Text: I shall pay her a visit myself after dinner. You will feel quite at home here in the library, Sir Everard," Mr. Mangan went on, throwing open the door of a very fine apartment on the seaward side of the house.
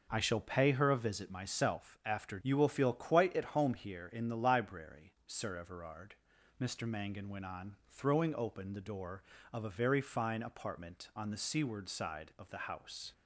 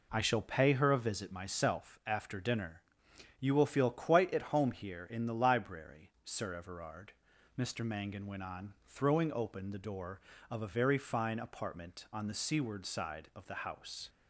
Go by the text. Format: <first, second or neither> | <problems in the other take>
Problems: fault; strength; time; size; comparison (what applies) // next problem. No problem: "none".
second | skips "dinner"; at 2.3 s